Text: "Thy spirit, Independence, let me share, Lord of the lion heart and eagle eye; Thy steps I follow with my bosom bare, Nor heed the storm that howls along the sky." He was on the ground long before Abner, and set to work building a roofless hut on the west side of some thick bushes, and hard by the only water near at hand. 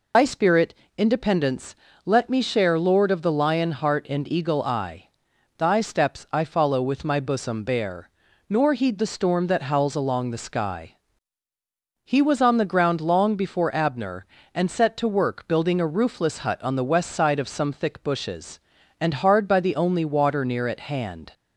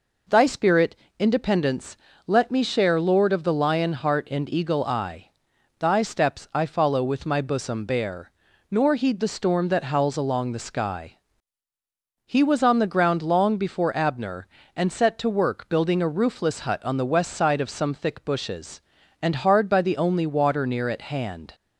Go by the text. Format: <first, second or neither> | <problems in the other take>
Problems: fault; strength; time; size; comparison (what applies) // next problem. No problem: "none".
second | loses the start of "Thy"; at 0.1 s; 80 ms